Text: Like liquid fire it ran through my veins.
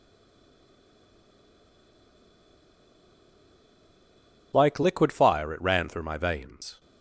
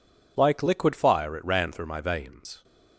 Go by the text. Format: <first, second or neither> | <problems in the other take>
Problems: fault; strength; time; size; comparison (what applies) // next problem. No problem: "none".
second | stays silent before the first word; strong; until 4.5 s; 4.5 s long